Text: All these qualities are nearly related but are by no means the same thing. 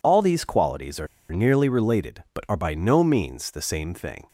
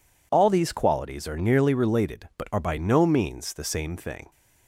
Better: second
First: pauses between "are" and "nearly"; slight; at 1.0 s; 0.25 s long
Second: none

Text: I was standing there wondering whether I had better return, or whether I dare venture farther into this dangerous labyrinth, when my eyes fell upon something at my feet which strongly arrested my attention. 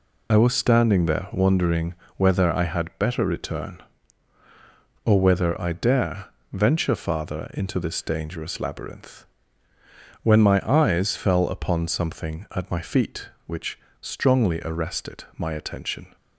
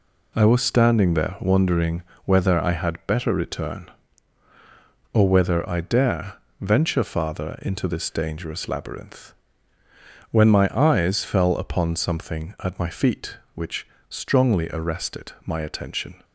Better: second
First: loses the start of "I"; at 0.3 s; 35 ms // pauses between "wondering" and "whether"; slight; at 1.9 s; 0.22 s long // pauses between "dare" and "venture"; slight; at 6.2 s; 0.22 s long // pauses between "which" and "strongly"; slight; at 13.7 s; 0.24 s long // pauses between "arrested" and "my"; slight; at 15.2 s; 0.16 s long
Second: pauses between "wondering" and "whether"; slight; at 2.0 s; 0.22 s long // pauses between "dare" and "venture"; slight; at 6.3 s; 0.22 s long // pauses between "which" and "strongly"; slight; at 13.8 s; 0.24 s long // pauses between "arrested" and "my"; slight; at 15.2 s; 0.16 s long

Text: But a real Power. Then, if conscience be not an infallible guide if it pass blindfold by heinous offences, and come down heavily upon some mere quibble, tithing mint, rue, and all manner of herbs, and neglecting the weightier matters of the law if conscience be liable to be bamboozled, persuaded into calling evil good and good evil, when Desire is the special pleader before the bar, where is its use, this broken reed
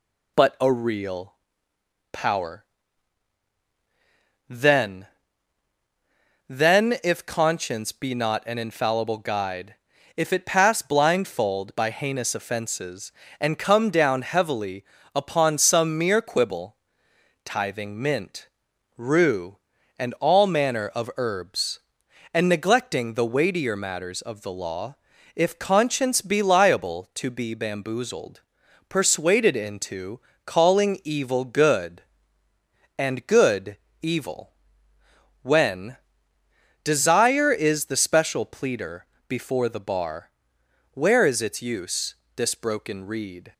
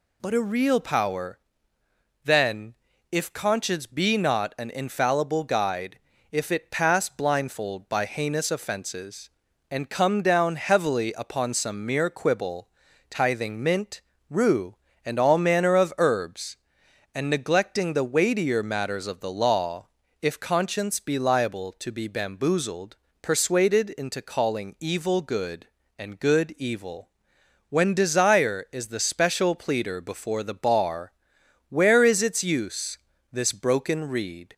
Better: second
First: pauses between "real" and "Power"; noticeable; at 1.3 s; 0.78 s long // says "Then" twice; at 6.4 s // pauses between "guide" and "if"; at 9.7 s; 0.42 s long // pauses between "heavily" and "upon"; slight; at 14.8 s; 0.28 s long // pauses between "law" and "if"; at 24.9 s; 0.40 s long // pauses between "into" and "calling"; slight; at 30.1 s; 0.26 s long // pauses between "good" and "evil"; slight; at 33.7 s; 0.24 s long // pauses between "when" and "Desire"; noticeable; at 35.9 s; 0.86 s long // pauses between "pleader" and "before"; slight; at 39.0 s; 0.22 s long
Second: pauses between "guide" and "if"; slight; at 5.9 s; 0.33 s long // pauses between "law" and "if"; slight; at 19.8 s; 0.34 s long

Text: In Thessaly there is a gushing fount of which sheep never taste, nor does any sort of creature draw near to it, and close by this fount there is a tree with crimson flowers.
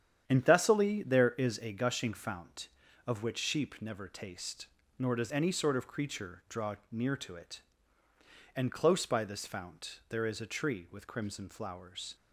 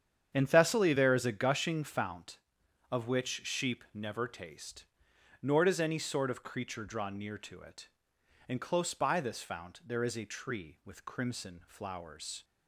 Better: neither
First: starts louder than the rest; strong; until 1.2 s; 9 dB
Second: starts louder than the rest; strong; until 1.3 s; 8.5 dB

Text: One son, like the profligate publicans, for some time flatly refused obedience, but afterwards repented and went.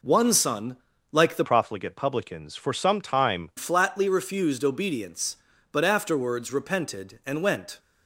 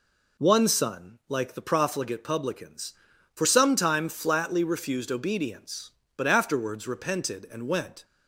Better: second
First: changes voice from "profligate" to "time"; from 1.4 to 3.5 s; 2.1 s long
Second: none

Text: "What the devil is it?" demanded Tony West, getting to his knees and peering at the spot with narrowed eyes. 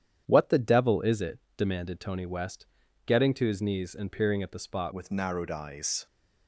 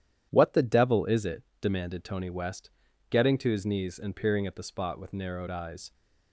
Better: second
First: starts louder than the rest; strong; until 1.2 s; 9.5 dB // changes voice at "with"; from 4.9 s on; 1.1 s long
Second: starts louder than the rest; strong; until 1.3 s; 10.5 dB

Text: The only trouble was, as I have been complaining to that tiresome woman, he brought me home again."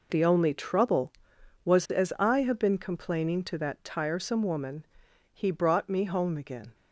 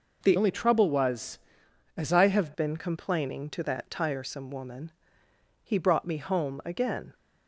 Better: first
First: none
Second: changes voice from "only" to "have"; from 0.3 to 2.5 s; 2.2 s long

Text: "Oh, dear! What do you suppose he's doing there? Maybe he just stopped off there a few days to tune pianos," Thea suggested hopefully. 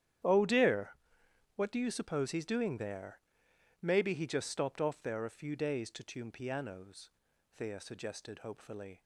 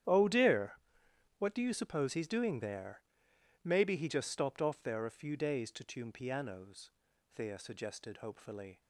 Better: neither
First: starts louder than the rest; strong; until 1.9 s; 10.5 dB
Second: starts louder than the rest; strong; until 1.7 s; 10.5 dB

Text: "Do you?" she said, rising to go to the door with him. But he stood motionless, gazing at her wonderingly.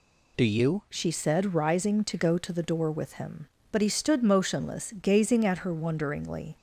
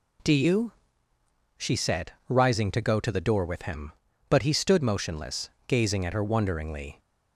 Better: second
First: changes voice at "she"; from 0.8 s on; 5.7 s long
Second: none

